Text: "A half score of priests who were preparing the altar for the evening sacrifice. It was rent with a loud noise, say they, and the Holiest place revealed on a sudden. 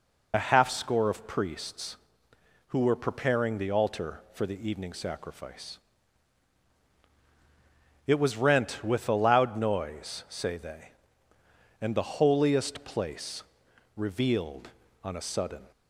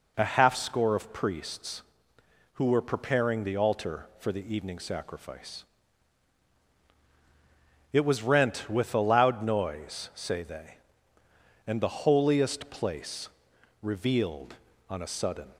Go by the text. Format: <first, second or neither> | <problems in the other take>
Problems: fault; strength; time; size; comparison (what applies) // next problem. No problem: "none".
second | loses the start of "A"; at 0.3 s; 30 ms // pauses between "place" and "revealed"; noticeable; at 13.4 s; 0.52 s long; noticeable in the second